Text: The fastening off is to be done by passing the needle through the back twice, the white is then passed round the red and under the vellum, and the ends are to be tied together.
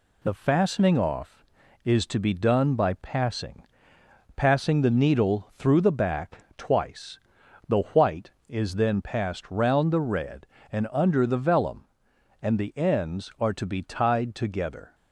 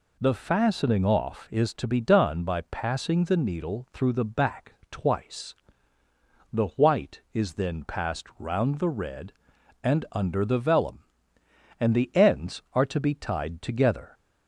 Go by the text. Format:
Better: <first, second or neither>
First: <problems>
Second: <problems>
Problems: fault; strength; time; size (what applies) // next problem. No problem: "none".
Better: second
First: says "passing" twice; at 4.3 s // pauses between "back" and "twice"; slight; at 6.3 s; 0.18 s long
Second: pauses between "back" and "twice"; slight; at 4.7 s; 0.18 s long